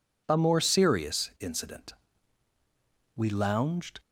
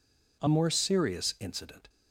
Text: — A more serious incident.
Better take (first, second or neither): second